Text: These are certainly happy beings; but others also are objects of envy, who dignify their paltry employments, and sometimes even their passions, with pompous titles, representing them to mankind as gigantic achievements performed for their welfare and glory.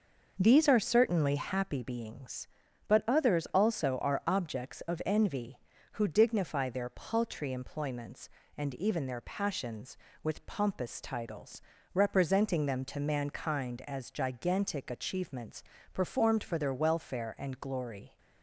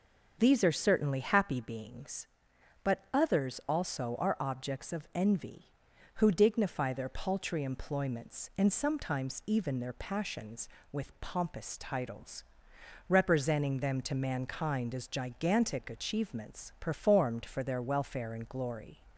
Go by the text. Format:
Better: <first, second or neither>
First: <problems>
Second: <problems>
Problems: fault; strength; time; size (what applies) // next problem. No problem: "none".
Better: second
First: starts louder than the rest; noticeable; until 1.4 s; 6 dB // skips "sometimes"; at 8.7 s // pauses between "achievements" and "performed"; slight; at 15.6 s; 0.28 s long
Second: starts louder than the rest; until 1.3 s; 6.5 dB